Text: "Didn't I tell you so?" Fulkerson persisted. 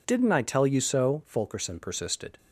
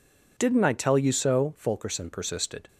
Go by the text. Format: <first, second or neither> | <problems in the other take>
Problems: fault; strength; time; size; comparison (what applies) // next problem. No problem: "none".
neither | none